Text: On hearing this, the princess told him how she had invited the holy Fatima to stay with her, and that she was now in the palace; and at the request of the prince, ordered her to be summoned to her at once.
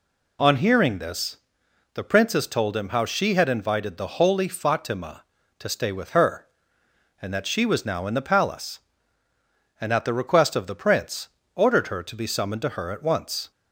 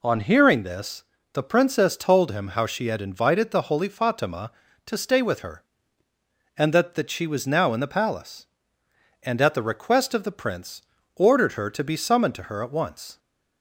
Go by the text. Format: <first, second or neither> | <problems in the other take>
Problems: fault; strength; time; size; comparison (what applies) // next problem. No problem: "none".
first | says "that" twice; at 6.9 s